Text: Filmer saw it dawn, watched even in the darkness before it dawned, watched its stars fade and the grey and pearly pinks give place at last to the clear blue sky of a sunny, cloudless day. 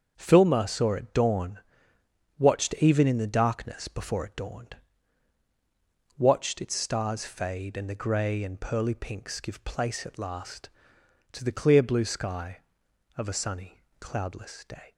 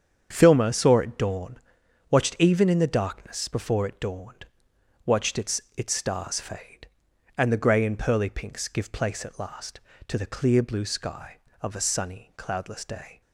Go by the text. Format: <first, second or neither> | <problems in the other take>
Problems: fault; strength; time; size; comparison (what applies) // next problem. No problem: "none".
first | starts louder than the rest; strong; until 1.3 s; 8 dB; also in the first // says "its" twice; at 5.7 s